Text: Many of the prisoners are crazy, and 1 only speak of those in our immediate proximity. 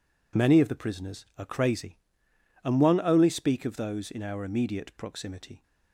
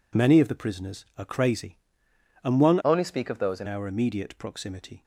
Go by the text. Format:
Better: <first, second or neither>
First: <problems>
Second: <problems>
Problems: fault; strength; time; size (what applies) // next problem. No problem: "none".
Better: first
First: none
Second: changes voice from "only" to "in"; from 2.8 to 3.6 s; 0.8 s long